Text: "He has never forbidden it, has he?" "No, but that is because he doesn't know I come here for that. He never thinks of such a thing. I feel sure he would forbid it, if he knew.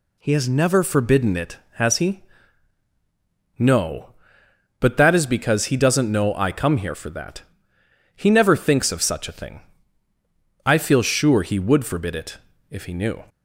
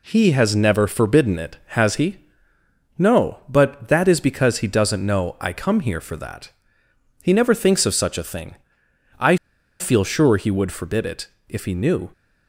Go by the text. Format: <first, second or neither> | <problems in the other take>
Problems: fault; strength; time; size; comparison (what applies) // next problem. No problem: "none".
first | pauses between "I" and "feel"; at 9.3 s; 0.42 s long